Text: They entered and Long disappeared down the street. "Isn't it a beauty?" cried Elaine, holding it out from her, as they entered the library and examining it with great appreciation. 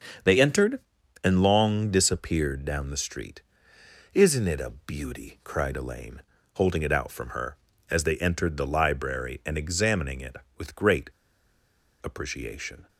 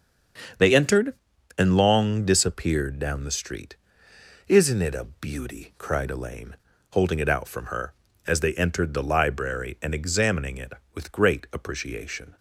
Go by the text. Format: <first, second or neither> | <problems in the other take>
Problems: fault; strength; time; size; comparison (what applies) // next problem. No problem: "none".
second | starts louder than the rest; strong; until 1.6 s; 7 dB; strong in the second // pauses between "great" and "appreciation"; noticeable; at 11.1 s; 0.93 s long